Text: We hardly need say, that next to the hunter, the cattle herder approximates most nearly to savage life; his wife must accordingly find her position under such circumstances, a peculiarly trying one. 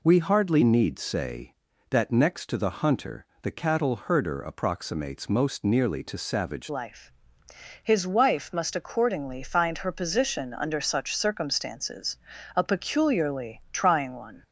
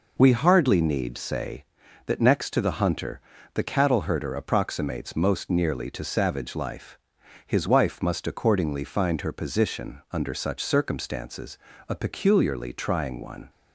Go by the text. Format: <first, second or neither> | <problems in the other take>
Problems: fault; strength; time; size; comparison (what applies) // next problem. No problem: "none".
second | changes voice at "life"; from 6.6 s on; 7.8 s long